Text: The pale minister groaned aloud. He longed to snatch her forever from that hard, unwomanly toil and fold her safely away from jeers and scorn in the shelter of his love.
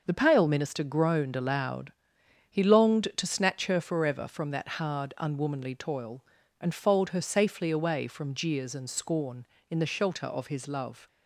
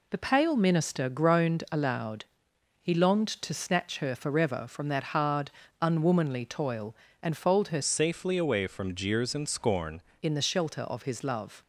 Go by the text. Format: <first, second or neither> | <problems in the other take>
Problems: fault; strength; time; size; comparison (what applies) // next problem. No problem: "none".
first | changes voice from "safely" to "scorn"; from 7.8 to 10.0 s; 2.2 s long